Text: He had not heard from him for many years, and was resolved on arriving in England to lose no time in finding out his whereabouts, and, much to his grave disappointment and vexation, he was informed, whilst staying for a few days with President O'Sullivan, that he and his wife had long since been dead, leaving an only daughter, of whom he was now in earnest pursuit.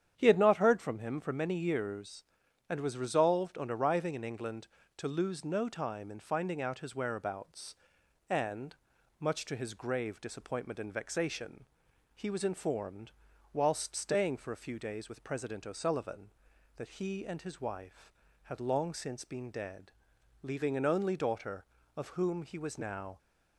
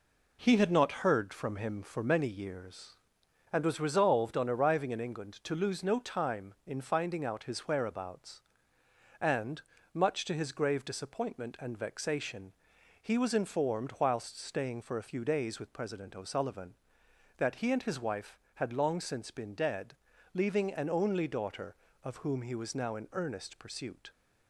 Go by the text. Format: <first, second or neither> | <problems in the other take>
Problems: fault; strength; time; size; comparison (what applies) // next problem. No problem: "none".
second | starts louder than the rest; strong; until 1.1 s; 9 dB // stops before "in earnest pursuit"; at 23.1 s